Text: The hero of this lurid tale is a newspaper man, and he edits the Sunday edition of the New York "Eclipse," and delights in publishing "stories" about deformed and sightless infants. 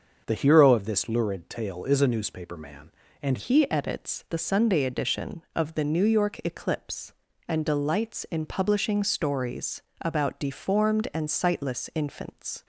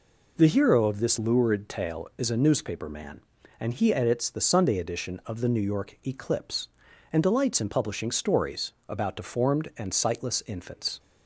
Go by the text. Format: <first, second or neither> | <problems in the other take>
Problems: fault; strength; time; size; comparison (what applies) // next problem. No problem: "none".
second | starts louder than the rest; until 1.2 s; 6.5 dB // changes voice at "he"; from 3.3 s on; 9.3 s long // pauses between "stories" and "about"; slight; at 9.8 s; 0.18 s long; slight in the second